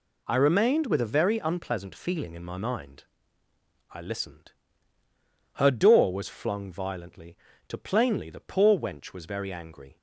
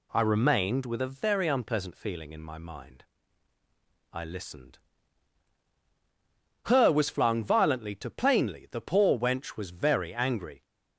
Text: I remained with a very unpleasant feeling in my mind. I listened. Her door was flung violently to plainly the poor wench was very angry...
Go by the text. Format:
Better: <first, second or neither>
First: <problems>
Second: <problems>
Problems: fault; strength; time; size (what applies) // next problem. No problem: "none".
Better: first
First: none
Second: skips "door"; at 6.9 s